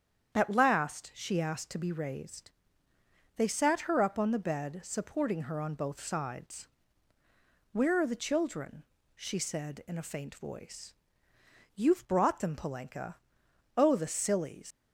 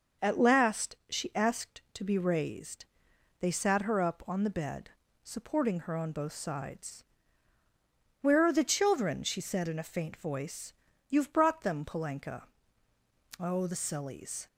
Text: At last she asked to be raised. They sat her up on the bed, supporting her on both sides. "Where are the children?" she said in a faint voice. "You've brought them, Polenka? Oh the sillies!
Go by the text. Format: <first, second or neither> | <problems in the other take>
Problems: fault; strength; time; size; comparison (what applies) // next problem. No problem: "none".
second | starts louder than the rest; strong; until 1.3 s; 8.5 dB // leaves "sillies" unfinished; at 14.7 s; 95 ms